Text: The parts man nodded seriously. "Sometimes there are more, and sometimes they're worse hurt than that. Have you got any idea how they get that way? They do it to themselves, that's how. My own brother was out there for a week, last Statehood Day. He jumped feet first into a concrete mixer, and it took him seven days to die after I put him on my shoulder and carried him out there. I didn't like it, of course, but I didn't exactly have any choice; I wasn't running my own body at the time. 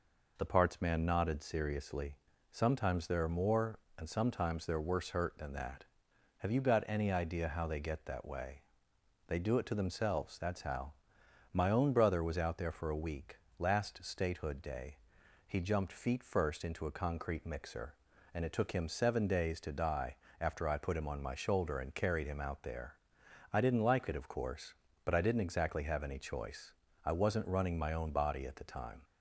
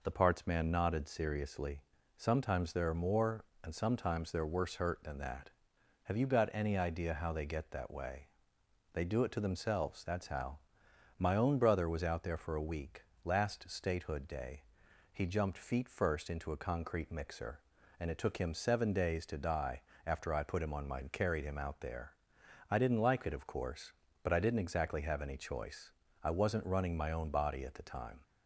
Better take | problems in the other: first | pauses between "die" and "after"; slight; at 19.8 s; 0.24 s long; slight in the first // skips "shoulder"; at 21.0 s

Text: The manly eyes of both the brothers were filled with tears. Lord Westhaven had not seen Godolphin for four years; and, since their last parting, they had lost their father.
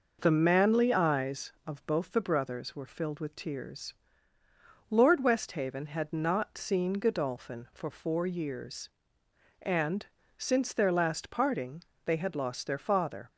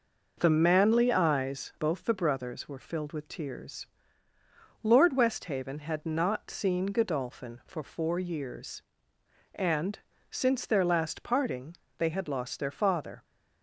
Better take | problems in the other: first | skips "of"; at 1.7 s

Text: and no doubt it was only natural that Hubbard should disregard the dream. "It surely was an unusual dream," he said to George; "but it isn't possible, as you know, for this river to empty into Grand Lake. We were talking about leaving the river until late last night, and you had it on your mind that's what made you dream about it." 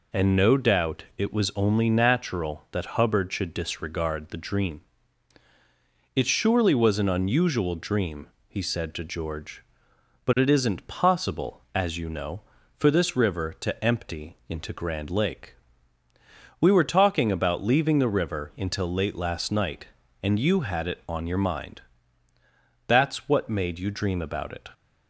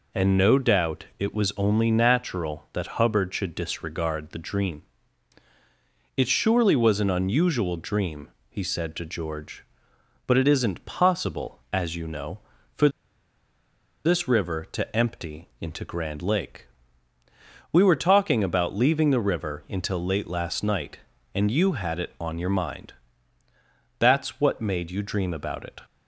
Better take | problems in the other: first | pauses between "for" and "this"; at 12.8 s; 1.1 s long // pauses between "mind" and "that's"; at 22.9 s; 1.0 s long; also in the first

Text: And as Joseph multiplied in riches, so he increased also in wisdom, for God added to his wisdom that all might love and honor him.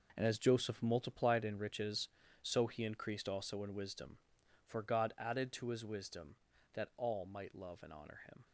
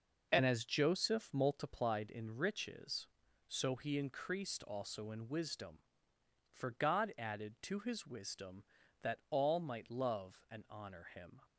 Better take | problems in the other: second | gets quieter; strong; throughout; 11 dB

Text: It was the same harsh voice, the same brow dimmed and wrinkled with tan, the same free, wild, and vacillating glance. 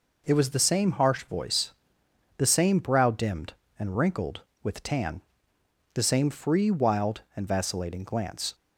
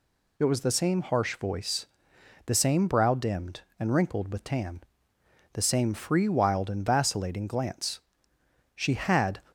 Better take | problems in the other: first | goes on to say "She had"; noticeable; from 8.7 s on; 0.66 s long

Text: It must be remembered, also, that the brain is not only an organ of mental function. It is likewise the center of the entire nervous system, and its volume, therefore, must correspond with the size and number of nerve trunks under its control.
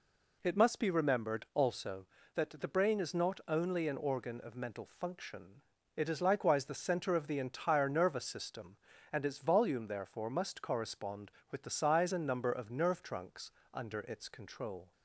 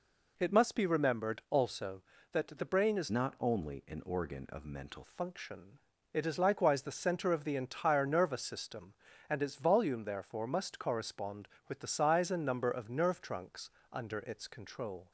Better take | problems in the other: first | changes voice from "not" to "mental"; from 3.0 to 5.0 s; 2.0 s long // pauses between "trunks" and "under"; slight; at 13.6 s; 0.22 s long; slight in the first

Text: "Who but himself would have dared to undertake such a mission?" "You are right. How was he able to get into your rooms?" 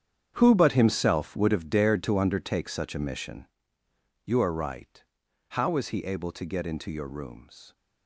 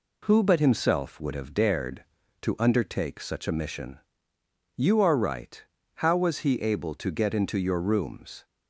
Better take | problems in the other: second | gets quieter; strong; throughout; 15 dB

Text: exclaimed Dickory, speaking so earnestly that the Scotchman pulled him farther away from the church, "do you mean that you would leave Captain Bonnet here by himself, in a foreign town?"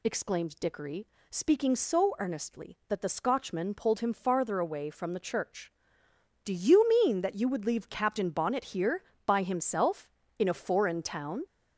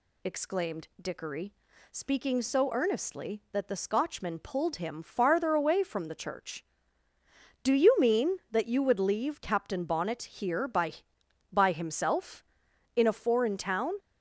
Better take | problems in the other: first | says "by" twice; at 11.5 s

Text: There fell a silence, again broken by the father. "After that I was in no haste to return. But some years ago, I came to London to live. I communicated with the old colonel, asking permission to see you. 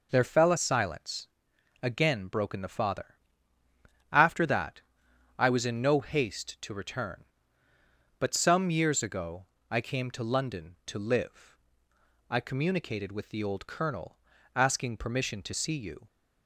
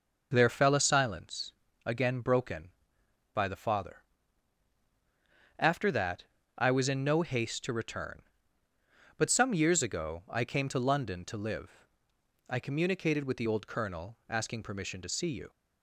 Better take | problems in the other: second | skips "by"; at 2.6 s // pauses between "that" and "I"; noticeable; at 4.7 s; 0.58 s long; slight in the second

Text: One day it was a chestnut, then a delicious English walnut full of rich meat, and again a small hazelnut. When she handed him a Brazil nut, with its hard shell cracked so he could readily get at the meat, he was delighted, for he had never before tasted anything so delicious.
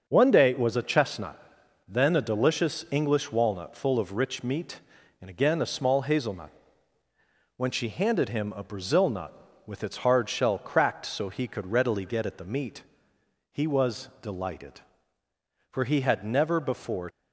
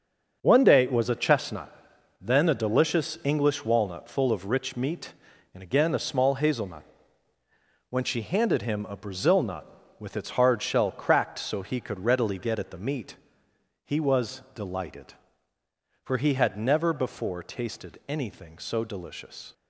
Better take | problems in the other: second | starts louder than the rest; until 1.0 s; 6.5 dB; also in the second // stops before "tasted anything so delicious"; at 17.0 s

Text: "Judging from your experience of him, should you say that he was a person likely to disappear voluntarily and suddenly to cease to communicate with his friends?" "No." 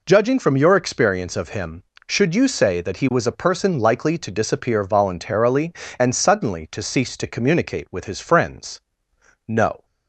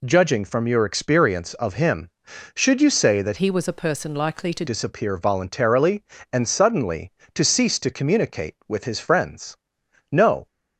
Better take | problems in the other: first | changes voice from "he" to "to"; from 3.3 to 4.6 s; 1.3 s long

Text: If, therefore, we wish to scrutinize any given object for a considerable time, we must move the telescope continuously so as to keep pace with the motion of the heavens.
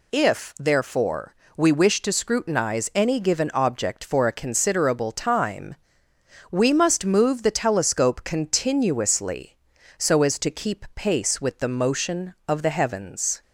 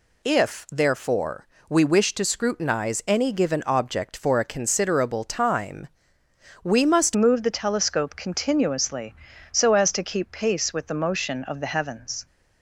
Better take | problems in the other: first | changes voice at "move"; from 7.1 s on; 5.1 s long

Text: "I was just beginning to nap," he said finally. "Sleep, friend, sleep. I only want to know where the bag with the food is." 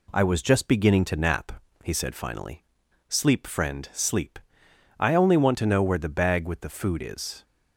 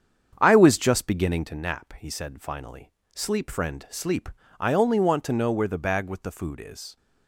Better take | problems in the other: first | starts louder than the rest; strong; until 1.6 s; 7.5 dB

